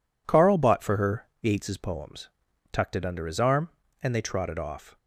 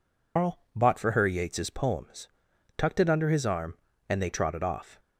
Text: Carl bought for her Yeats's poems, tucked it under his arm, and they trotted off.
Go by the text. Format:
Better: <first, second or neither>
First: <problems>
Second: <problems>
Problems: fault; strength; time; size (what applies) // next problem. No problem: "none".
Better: first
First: none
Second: loses the start of "Carl"; at 0.3 s; 170 ms // pauses between "Carl" and "bought"; slight; at 0.5 s; 0.16 s long